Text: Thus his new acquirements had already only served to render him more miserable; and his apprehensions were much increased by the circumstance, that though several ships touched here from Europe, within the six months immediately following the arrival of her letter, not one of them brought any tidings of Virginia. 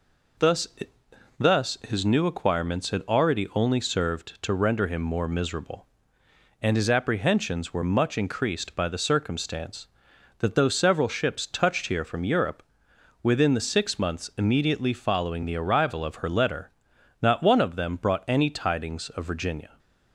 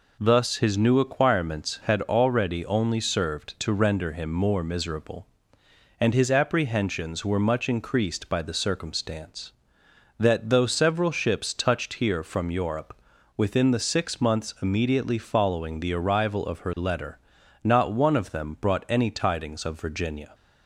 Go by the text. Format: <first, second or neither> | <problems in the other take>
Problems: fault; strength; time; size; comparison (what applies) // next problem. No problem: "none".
second | says "Thus" twice; at 1.3 s